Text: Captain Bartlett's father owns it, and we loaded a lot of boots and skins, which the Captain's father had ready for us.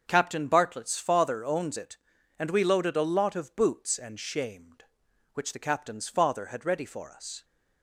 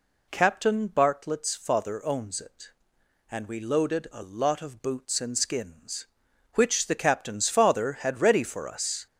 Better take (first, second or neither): second